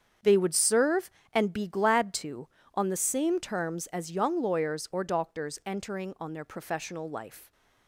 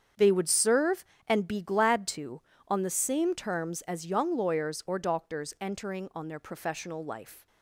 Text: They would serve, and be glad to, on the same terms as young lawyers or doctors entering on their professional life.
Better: neither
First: starts louder than the rest; strong; until 1.4 s; 7.5 dB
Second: starts louder than the rest; strong; until 1.4 s; 7.5 dB

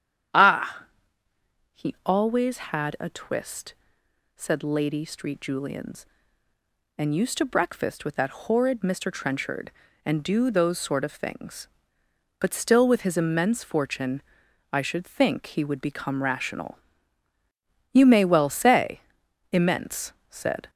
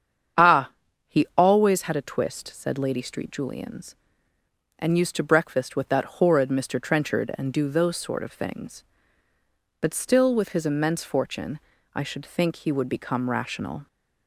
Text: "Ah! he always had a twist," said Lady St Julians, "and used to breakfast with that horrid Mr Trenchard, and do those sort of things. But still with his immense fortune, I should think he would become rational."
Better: second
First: starts louder than the rest; strong; until 2.3 s; 9.5 dB // goes on to say "You may well say immense said"; strong; from 17.9 s on; 2.7 s long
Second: starts louder than the rest; strong; until 1.8 s; 8 dB

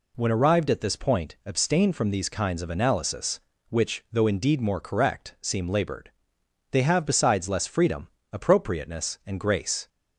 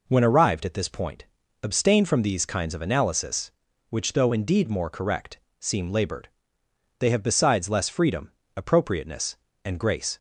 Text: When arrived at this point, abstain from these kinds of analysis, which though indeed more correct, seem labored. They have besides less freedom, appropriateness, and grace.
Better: neither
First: none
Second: none

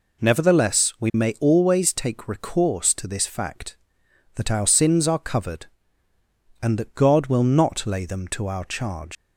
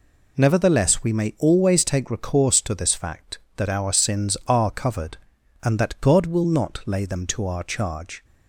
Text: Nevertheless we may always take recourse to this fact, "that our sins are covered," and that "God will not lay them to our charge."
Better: second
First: leaves "charge" unfinished; at 9.1 s; 150 ms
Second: none

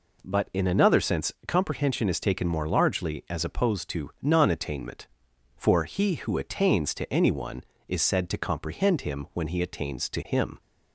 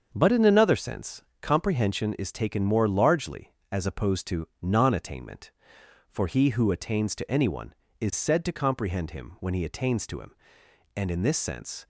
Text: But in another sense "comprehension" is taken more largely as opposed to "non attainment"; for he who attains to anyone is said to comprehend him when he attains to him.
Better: first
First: pauses between "sense" and "comprehension"; slight; at 1.3 s; 0.16 s long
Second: starts louder than the rest; until 1.1 s; 7 dB // pauses between "sense" and "comprehension"; slight; at 1.2 s; 0.20 s long // goes on to say "And in this sense"; noticeable; from 10.9 s on; 0.92 s long

